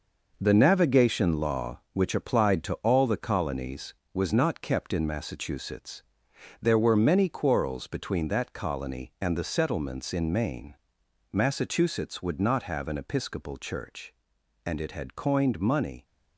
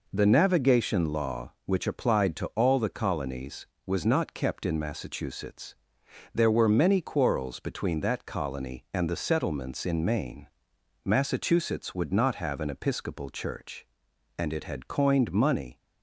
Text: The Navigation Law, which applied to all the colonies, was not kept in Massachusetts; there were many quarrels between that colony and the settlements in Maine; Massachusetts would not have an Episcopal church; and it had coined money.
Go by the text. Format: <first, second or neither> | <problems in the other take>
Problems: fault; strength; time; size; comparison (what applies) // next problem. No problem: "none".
second | gets quieter; strong; throughout; 8 dB